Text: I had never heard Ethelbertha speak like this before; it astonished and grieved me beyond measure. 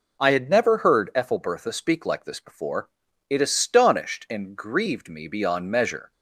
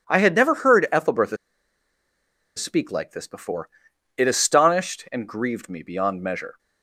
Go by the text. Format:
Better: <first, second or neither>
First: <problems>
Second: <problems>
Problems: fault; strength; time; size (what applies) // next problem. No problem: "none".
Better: first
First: none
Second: pauses between "Ethelbertha" and "speak"; at 1.3 s; 1.2 s long